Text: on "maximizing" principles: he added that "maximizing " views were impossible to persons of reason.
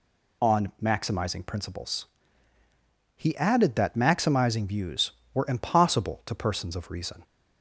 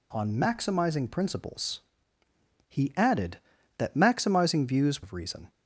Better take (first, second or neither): first